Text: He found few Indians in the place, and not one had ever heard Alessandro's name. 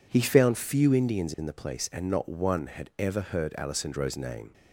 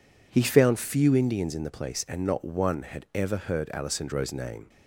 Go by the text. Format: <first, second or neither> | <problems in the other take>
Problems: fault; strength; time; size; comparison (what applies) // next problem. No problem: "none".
neither | none